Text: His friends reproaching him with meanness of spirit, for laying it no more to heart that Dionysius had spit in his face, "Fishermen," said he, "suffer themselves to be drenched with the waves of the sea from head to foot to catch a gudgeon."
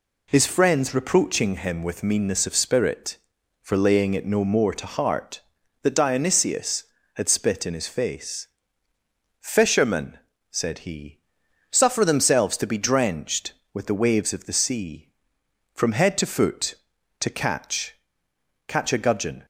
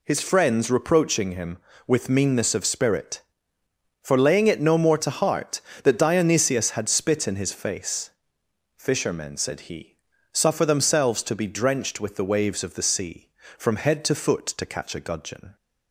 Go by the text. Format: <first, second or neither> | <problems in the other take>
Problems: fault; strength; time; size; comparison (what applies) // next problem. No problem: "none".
second | says "catch" twice; at 18.6 s